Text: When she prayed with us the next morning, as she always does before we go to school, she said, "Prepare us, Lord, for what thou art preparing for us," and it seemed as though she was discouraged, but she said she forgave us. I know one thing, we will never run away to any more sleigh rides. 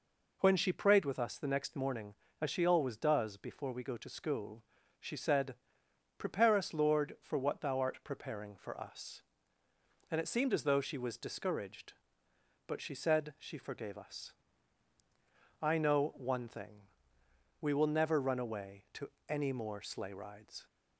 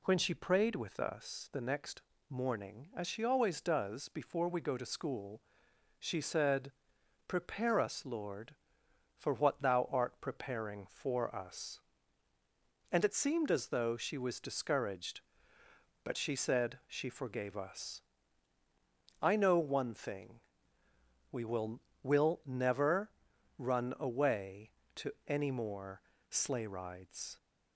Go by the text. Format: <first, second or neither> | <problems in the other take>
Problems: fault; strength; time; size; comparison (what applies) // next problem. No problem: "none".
first | pauses between "next" and "morning"; slight; at 2.0 s; 0.28 s long // says "will" twice; at 22.0 s // pauses between "never" and "run"; noticeable; at 23.0 s; 0.48 s long // pauses between "to" and "any"; slight; at 25.1 s; 0.16 s long; slight in the first // pauses between "more" and "sleigh"; slight; at 26.0 s; 0.28 s long